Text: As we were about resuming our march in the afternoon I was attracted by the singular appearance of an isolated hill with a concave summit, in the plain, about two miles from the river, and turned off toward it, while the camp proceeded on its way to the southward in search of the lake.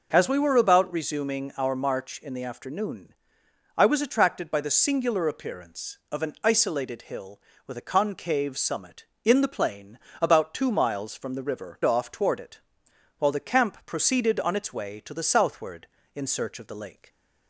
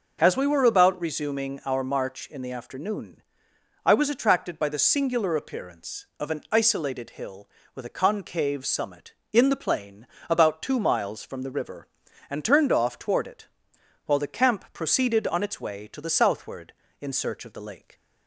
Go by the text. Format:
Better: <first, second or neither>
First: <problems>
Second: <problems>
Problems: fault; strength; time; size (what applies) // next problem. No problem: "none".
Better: second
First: pauses between "afternoon" and "I"; noticeable; at 3.1 s; 0.64 s long // skips "and turned"; at 11.8 s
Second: pauses between "afternoon" and "I"; noticeable; at 3.2 s; 0.64 s long